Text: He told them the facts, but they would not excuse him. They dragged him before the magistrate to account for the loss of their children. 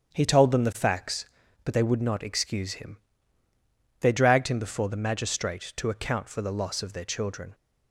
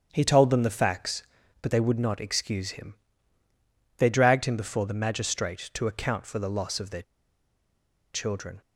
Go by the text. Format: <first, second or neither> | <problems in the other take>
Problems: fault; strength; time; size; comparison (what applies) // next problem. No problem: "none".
first | starts louder than the rest; strong; until 1.1 s; 8 dB; strong in the first // pauses between "their" and "children"; at 7.0 s; 1.1 s long